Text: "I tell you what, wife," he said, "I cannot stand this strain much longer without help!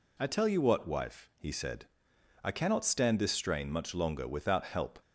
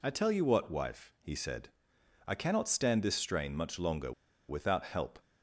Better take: first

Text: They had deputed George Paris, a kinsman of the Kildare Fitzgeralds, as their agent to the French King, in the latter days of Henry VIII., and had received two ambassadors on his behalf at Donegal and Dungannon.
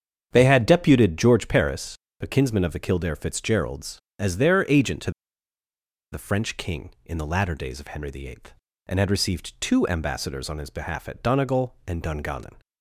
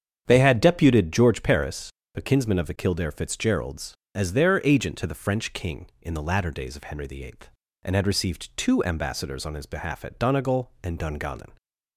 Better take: second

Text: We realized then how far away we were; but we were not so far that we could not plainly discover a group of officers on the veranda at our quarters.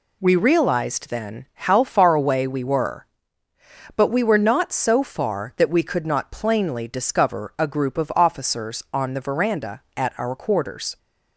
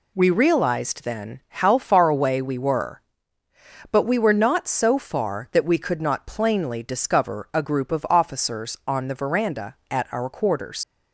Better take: first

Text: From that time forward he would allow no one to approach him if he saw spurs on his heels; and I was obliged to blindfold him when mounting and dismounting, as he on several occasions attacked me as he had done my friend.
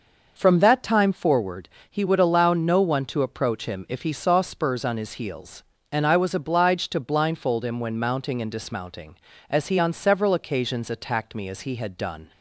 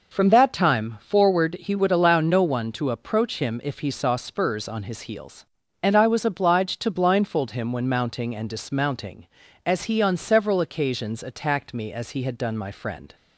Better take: second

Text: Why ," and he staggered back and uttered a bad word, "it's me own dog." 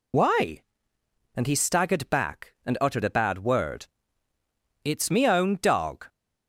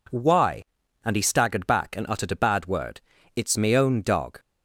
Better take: second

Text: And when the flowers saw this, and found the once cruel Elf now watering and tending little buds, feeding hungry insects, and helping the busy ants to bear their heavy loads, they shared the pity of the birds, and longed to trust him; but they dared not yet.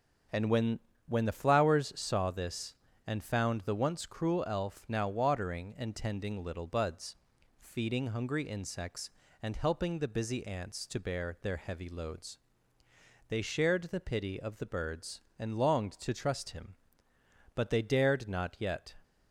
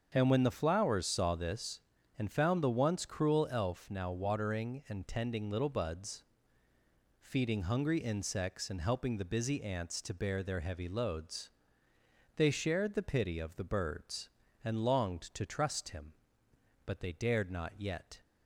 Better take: second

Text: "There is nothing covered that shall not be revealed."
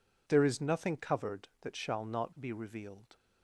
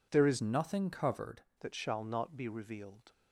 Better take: first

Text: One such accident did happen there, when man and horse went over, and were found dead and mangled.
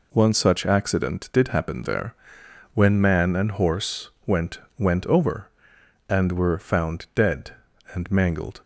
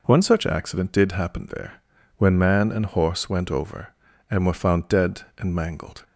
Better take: second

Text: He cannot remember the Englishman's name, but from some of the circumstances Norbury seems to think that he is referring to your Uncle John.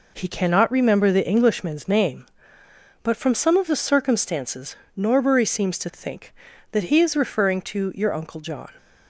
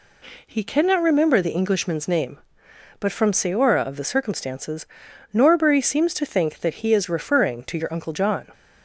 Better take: first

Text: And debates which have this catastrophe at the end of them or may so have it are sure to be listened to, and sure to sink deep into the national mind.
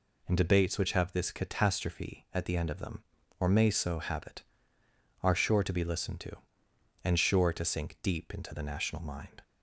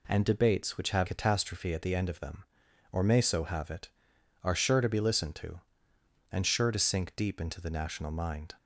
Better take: first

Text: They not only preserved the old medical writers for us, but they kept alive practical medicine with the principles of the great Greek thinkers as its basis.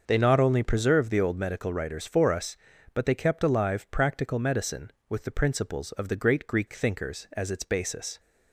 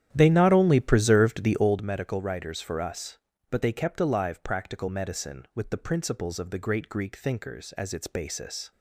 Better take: first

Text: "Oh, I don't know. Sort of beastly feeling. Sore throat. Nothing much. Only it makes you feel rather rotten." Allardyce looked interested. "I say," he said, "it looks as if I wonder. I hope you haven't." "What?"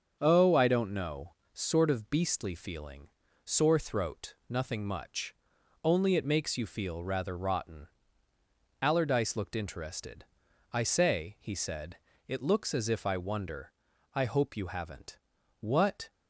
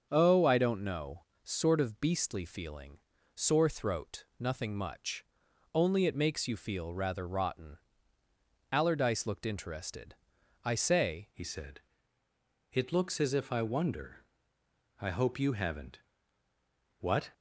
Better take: first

